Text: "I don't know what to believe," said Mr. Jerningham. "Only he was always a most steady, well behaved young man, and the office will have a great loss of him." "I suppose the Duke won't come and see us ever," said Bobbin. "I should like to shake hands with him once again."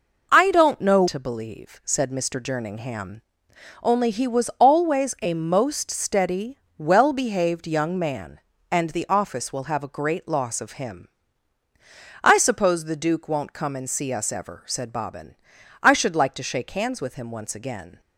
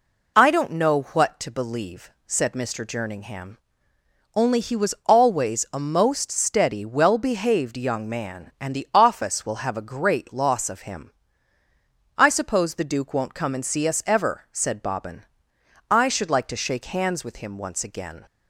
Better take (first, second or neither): second